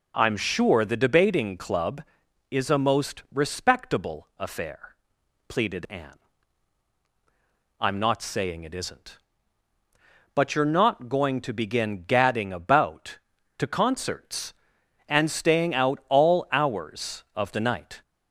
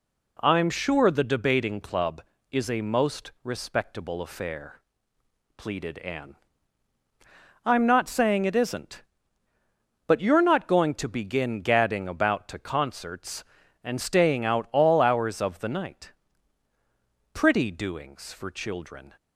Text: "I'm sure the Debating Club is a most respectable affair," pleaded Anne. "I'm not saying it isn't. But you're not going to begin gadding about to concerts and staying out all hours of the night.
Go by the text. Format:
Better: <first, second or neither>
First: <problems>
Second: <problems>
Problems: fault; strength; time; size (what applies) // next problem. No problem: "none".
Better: first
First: none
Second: goes on to say "Pretty doings for children"; strong; from 17.3 s on; 1.8 s long